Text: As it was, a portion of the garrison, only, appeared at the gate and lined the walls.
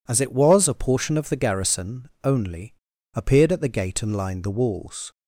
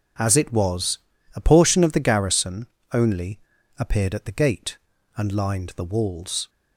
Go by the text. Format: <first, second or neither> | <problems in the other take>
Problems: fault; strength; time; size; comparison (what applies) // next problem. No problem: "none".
neither | none